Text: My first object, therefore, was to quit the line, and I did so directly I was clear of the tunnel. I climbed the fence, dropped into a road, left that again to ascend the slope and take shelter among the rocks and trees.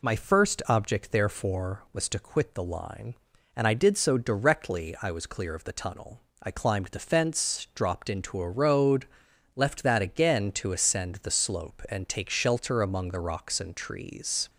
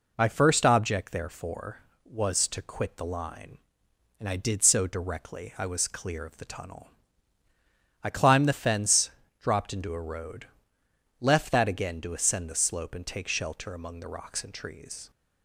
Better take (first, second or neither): neither